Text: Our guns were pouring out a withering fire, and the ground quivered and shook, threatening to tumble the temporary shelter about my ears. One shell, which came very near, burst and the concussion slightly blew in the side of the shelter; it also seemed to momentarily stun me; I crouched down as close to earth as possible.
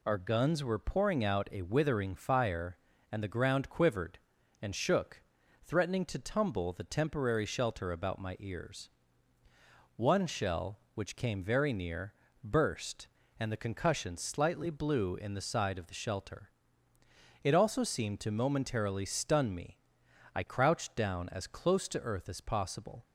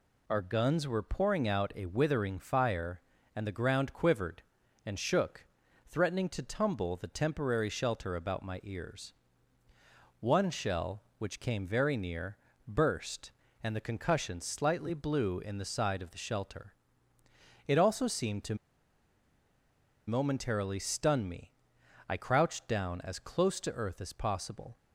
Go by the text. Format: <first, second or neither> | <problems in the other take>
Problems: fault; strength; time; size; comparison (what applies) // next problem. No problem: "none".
first | pauses between "to" and "momentarily"; strong; at 18.5 s; 1.5 s long